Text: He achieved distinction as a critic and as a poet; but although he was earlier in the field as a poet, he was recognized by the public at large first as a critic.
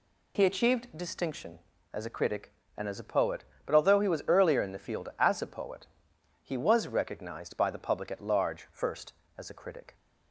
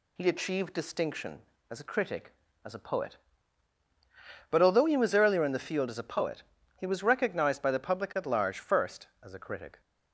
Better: first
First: none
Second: skips "and"; at 2.4 s

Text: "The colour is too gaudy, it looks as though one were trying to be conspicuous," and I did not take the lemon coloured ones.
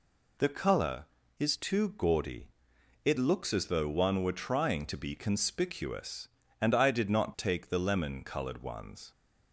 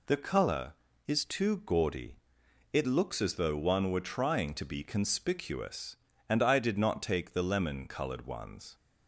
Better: neither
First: none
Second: none

